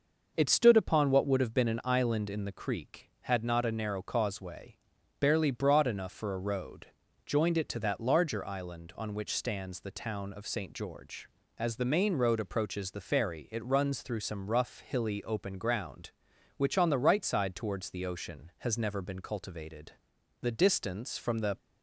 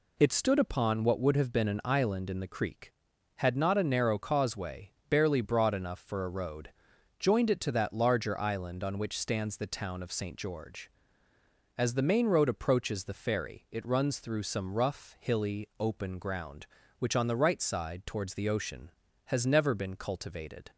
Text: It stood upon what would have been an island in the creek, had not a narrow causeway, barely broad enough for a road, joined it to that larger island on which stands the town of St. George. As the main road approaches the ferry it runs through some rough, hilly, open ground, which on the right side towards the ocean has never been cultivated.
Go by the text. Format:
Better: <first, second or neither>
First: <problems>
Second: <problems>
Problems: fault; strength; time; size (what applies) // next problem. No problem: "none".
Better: second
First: starts louder than the rest; noticeable; until 1.3 s; 6 dB // goes on to say "The distance from the"; noticeable; from 20.4 s on; 1.1 s long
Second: none